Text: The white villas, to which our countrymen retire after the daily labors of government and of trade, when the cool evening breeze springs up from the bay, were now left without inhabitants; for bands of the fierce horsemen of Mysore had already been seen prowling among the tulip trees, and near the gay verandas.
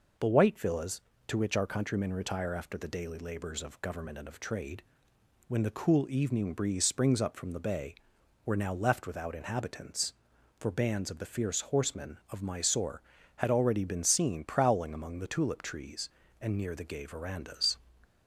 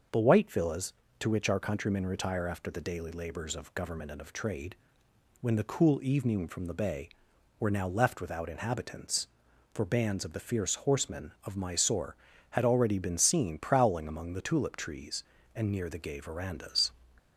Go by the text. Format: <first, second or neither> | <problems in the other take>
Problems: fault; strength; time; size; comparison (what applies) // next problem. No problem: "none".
first | starts louder than the rest; noticeable; until 1.4 s; 6 dB // skips "breeze springs up"; at 6.4 s